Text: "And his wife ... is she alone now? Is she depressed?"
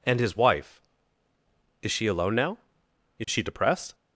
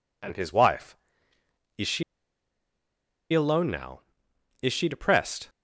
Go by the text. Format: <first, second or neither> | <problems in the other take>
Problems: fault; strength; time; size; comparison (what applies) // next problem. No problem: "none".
first | pauses between "she" and "alone"; strong; at 2.0 s; 1.3 s long